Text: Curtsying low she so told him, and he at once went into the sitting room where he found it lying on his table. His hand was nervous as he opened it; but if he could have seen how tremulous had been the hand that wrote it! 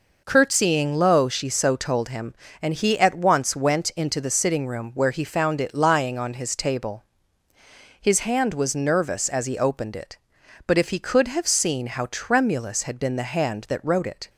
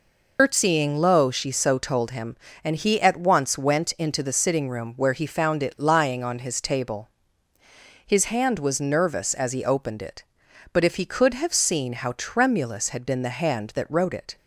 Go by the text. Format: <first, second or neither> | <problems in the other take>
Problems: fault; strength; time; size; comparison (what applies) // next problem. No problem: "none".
first | loses the start of "Curtsying"; at 0.3 s; 125 ms